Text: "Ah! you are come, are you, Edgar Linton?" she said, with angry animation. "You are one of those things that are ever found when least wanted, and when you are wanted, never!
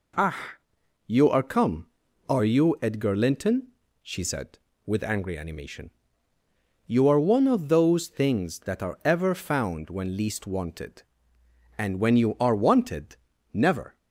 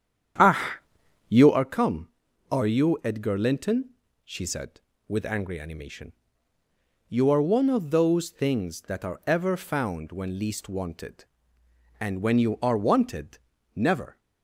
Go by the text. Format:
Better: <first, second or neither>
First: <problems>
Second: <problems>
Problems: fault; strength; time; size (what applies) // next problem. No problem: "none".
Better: first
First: none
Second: starts louder than the rest; strong; until 1.6 s; 9 dB